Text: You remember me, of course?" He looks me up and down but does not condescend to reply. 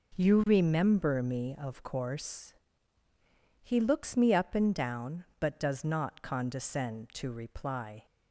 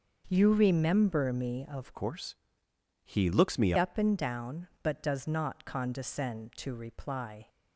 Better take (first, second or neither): first